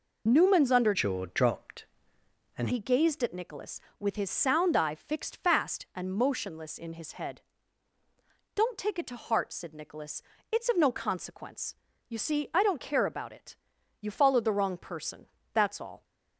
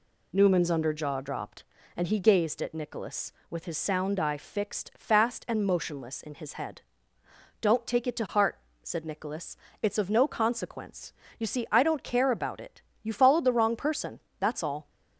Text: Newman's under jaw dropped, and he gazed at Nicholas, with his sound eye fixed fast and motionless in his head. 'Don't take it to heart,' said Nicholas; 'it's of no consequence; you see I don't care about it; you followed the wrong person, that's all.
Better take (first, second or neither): second